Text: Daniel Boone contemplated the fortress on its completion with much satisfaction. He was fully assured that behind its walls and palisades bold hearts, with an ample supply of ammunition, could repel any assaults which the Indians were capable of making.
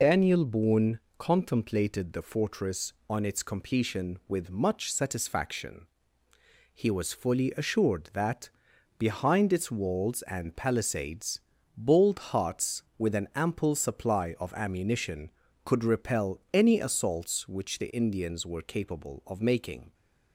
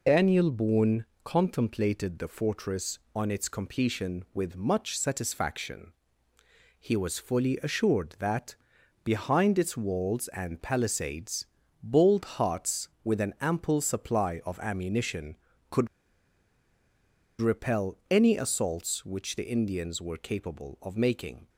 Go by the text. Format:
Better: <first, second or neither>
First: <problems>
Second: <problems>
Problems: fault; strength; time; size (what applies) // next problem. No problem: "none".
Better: first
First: pauses between "Boone" and "contemplated"; slight; at 0.9 s; 0.22 s long // pauses between "that" and "behind"; noticeable; at 8.4 s; 0.48 s long // pauses between "palisades" and "bold"; at 11.3 s; 0.38 s long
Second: pauses between "Boone" and "contemplated"; slight; at 1.0 s; 0.22 s long // pauses between "that" and "behind"; noticeable; at 8.5 s; 0.48 s long // pauses between "palisades" and "bold"; at 11.4 s; 0.38 s long // pauses between "could" and "repel"; strong; at 15.8 s; 1.5 s long